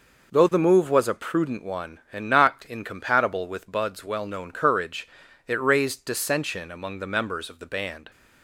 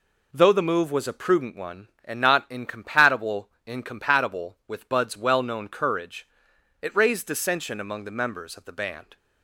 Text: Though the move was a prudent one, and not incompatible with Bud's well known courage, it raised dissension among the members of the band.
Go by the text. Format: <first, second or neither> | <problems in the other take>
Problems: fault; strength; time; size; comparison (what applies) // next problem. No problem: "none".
first | says "incompatible" twice; at 3.6 s